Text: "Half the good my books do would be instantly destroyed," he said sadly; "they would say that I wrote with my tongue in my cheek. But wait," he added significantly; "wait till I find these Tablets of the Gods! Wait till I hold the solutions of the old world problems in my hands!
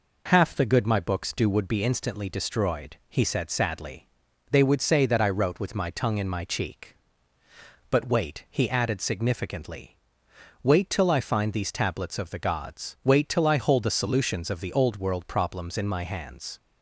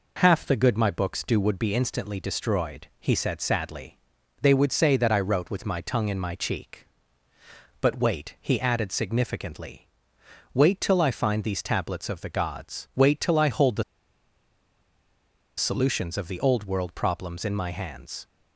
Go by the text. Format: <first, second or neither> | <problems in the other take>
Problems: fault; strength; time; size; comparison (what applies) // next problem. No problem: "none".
first | pauses between "the" and "solutions"; strong; at 13.8 s; 1.7 s long